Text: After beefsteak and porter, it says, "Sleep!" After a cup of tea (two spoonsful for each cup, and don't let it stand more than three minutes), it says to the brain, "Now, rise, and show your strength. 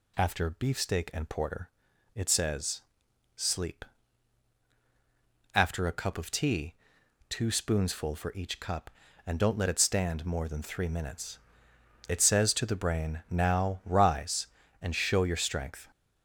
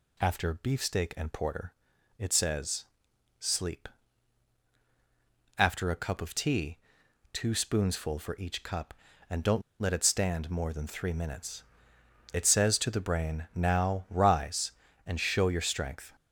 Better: first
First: none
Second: pauses between "don't" and "let"; slight; at 9.6 s; 0.19 s long

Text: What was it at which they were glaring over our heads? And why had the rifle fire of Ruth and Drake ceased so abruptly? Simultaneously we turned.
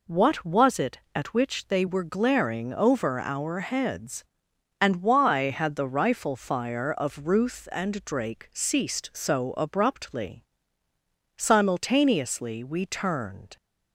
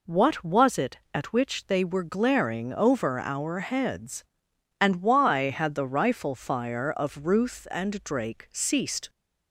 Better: first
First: none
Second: stops before "so abruptly Simultaneously we turned"; at 9.0 s

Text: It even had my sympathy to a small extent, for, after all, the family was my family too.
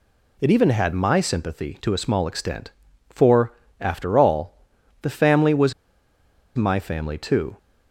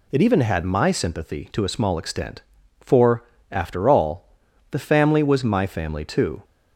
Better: second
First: pauses between "was" and "my"; noticeable; at 5.7 s; 0.82 s long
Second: none

